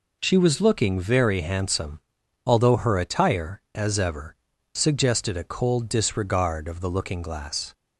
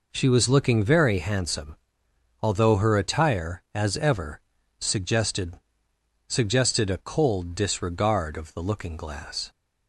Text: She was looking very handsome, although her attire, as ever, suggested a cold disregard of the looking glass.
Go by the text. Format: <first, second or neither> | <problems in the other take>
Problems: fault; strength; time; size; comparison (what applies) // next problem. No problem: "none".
first | says "suggested" twice; at 6.3 s